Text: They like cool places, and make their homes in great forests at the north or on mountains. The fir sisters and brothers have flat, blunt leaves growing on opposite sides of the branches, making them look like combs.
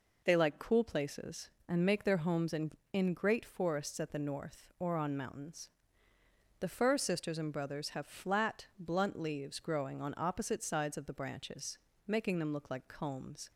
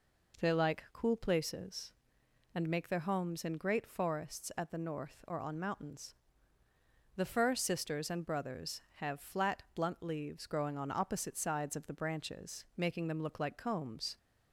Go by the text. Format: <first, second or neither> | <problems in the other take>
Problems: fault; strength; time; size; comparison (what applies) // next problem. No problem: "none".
second | says "in" twice; at 2.9 s